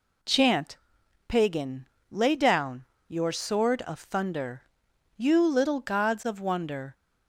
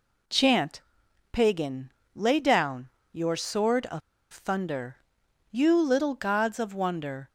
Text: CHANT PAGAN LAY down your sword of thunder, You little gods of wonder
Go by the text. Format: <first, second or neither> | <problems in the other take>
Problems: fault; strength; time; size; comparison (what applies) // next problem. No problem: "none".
first | pauses between "CHANT" and "PAGAN"; noticeable; at 0.8 s; 0.50 s long; noticeable in the first // pauses between "PAGAN" and "LAY"; slight; at 1.9 s; 0.24 s long; slight in the first // pauses between "down" and "your"; slight; at 2.8 s; 0.22 s long; slight in the first // pauses between "of" and "thunder"; slight; at 4.0 s; 0.31 s long